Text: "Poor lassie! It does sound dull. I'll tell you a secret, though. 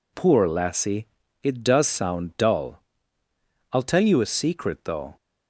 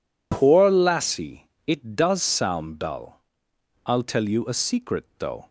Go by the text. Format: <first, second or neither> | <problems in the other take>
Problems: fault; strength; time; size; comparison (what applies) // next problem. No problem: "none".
neither | none